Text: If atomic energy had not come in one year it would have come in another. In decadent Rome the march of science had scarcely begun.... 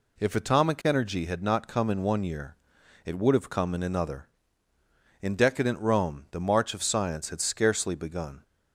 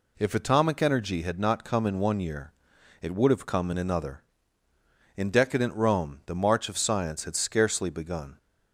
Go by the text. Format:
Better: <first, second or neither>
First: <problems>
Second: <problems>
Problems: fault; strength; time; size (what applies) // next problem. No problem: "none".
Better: neither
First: pauses between "year" and "it"; noticeable; at 2.5 s; 0.48 s long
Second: pauses between "year" and "it"; noticeable; at 2.5 s; 0.48 s long